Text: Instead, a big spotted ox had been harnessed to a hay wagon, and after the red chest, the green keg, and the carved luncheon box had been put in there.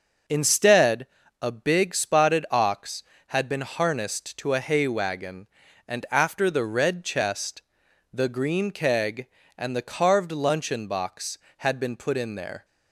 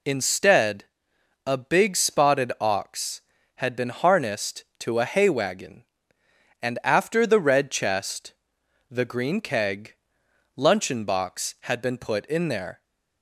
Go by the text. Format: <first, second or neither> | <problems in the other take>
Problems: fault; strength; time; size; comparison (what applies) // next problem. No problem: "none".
first | skips "and the carved"; at 10.2 s